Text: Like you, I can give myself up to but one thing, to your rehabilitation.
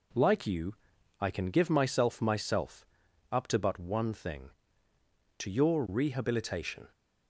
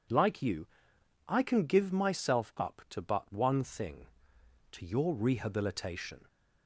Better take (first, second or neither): second